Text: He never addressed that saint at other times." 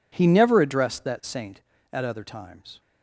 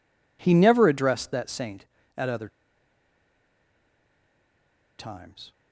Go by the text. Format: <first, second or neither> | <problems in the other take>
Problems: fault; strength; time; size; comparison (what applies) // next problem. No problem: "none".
first | pauses between "other" and "times"; strong; at 2.4 s; 2.5 s long